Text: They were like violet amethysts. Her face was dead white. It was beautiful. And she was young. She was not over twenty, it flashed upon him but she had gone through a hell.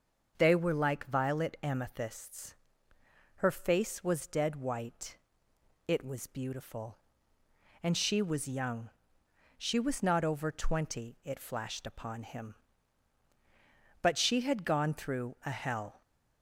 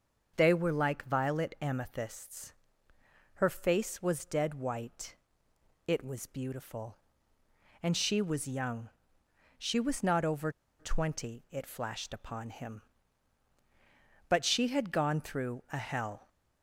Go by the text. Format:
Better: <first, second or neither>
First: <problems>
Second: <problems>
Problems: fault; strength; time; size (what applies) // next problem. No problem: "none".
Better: first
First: starts louder than the rest; until 1.3 s; 6.5 dB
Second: starts louder than the rest; until 1.3 s; 6.5 dB // pauses between "over" and "twenty"; slight; at 10.5 s; 0.27 s long